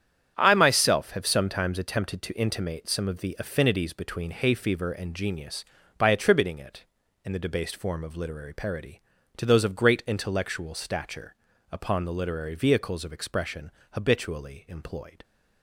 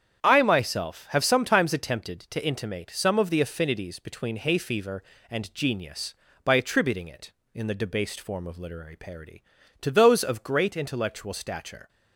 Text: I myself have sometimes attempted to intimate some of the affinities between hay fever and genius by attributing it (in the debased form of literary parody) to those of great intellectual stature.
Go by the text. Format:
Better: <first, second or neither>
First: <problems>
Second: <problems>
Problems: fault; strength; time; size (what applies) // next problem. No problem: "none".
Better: second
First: starts louder than the rest; strong; until 1.3 s; 9 dB // goes on to say "Upon the literary vehicles of expression habitually employed"; strong; from 11.7 s on; 3.5 s long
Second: starts louder than the rest; strong; until 1.2 s; 8.5 dB